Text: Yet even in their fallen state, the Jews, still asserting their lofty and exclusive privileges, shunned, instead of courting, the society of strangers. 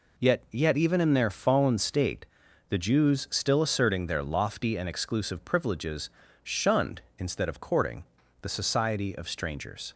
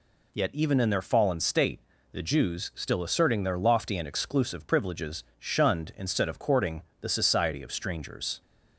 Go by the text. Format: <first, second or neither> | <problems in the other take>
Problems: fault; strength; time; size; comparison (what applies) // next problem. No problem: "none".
second | says "Yet" twice; at 0.5 s